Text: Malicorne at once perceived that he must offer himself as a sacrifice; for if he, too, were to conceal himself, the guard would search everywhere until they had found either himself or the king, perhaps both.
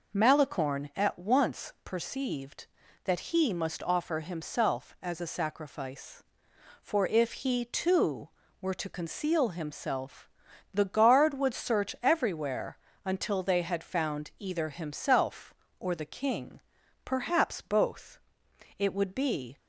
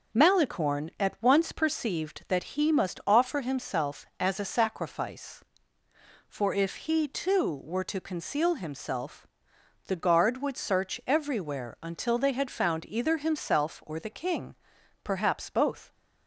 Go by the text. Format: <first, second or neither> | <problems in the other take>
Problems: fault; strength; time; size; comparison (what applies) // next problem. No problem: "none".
second | pauses between "everywhere" and "until"; slight; at 12.7 s; 0.28 s long // goes on to say "It would be"; noticeable; from 18.7 s on; 0.80 s long